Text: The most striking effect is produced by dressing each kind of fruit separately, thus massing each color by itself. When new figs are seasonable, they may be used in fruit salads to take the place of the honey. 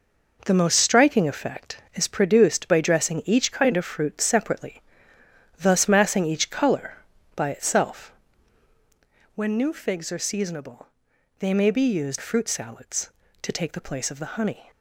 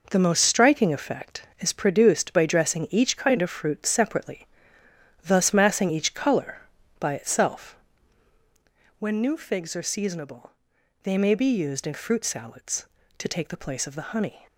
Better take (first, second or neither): second